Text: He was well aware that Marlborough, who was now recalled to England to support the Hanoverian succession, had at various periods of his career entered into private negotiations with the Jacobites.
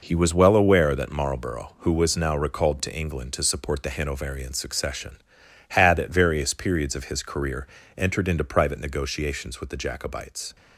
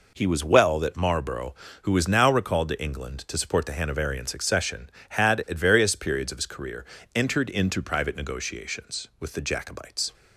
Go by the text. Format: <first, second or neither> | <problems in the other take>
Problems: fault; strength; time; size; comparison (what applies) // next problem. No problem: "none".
first | skips "aware"; at 0.7 s // pauses between "career" and "entered"; slight; at 6.8 s; 0.28 s long; slight in the first